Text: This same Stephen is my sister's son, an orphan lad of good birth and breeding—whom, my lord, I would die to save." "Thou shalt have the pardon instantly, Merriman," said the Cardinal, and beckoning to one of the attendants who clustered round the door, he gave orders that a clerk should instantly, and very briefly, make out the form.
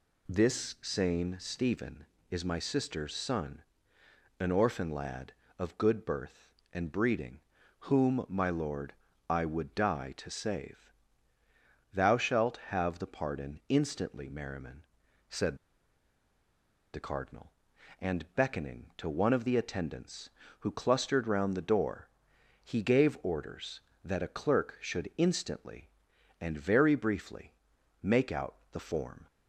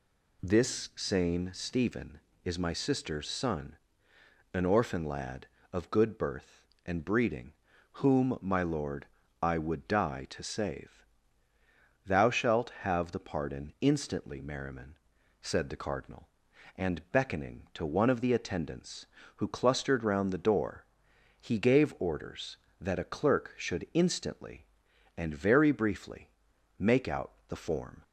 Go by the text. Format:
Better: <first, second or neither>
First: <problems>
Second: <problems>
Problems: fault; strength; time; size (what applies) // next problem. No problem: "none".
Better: second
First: pauses between "said" and "the"; strong; at 15.5 s; 1.3 s long // pauses between "out" and "the"; slight; at 28.5 s; 0.16 s long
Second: pauses between "out" and "the"; slight; at 27.3 s; 0.16 s long